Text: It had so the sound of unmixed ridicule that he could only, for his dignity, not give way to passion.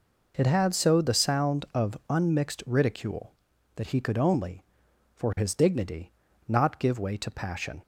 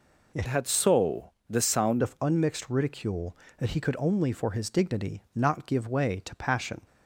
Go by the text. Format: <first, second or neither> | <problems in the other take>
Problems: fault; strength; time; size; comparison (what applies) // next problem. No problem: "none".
first | changes voice from "had" to "sound"; from 0.4 to 2.0 s; 1.6 s long // pauses between "so" and "the"; slight; at 1.3 s; 0.16 s long